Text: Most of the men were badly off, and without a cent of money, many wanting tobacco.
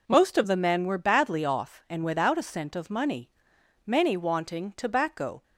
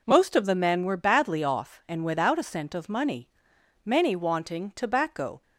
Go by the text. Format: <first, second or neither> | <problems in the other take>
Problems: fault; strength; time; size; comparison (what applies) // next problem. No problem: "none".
neither | none